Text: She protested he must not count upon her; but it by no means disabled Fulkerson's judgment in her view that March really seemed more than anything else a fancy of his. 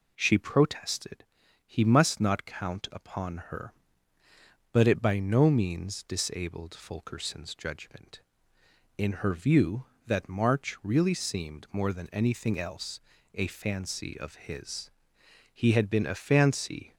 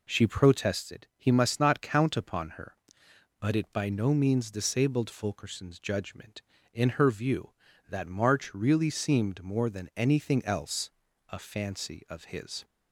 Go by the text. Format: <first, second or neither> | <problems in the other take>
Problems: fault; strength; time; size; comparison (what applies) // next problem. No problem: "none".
second | pauses between "protested" and "he"; noticeable; at 1.2 s; 0.46 s long // pauses between "else" and "a"; slight; at 12.9 s; 0.36 s long; also in the second // goes on to say "He had been a fancy"; from 15.5 s on; 1.4 s long